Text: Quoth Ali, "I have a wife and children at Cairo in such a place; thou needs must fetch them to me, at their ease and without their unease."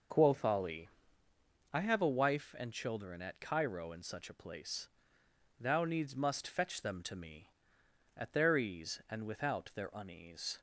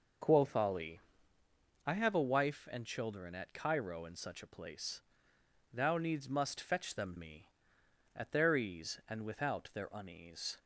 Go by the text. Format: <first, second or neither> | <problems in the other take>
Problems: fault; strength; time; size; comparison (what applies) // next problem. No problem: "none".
first | skips "to"; at 7.1 s